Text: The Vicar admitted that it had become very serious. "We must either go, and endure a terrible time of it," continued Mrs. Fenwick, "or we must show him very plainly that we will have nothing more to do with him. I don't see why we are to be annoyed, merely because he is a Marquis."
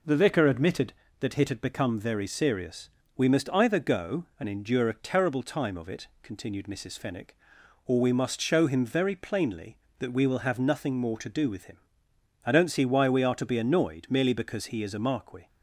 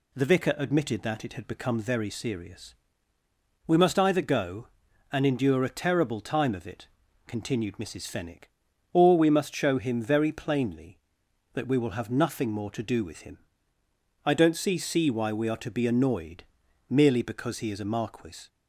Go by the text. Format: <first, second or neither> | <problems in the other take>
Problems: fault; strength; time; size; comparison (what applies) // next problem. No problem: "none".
first | says "see" twice; at 14.7 s